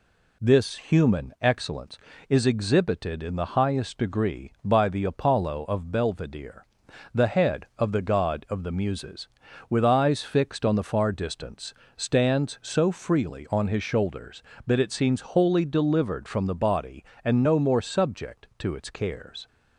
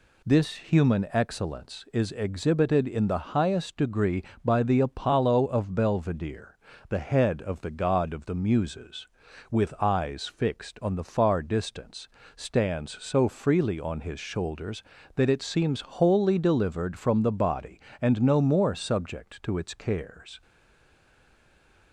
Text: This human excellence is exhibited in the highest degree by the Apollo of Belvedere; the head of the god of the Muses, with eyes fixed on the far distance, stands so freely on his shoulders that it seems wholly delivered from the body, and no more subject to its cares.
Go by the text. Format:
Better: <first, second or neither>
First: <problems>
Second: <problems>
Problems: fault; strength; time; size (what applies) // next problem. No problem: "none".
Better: first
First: none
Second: stays silent after the last word; noticeable; from 20.4 s on; 1.5 s long